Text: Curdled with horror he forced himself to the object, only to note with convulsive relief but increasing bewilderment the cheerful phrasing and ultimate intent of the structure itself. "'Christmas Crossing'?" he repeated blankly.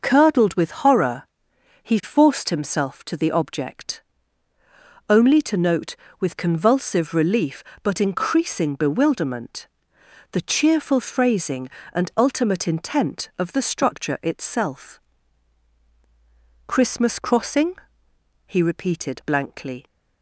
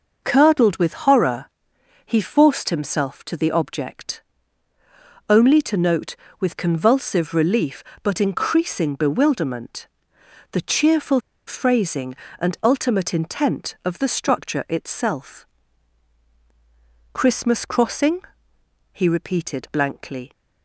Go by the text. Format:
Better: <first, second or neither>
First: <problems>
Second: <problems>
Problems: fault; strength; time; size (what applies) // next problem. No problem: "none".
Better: first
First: pauses between "horror" and "he"; noticeable; at 1.2 s; 0.56 s long // pauses between "bewilderment" and "the"; noticeable; at 9.6 s; 0.66 s long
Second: pauses between "horror" and "he"; noticeable; at 1.4 s; 0.56 s long // pauses between "bewilderment" and "the"; noticeable; at 9.8 s; 0.66 s long // pauses between "cheerful" and "phrasing"; slight; at 11.1 s; 0.28 s long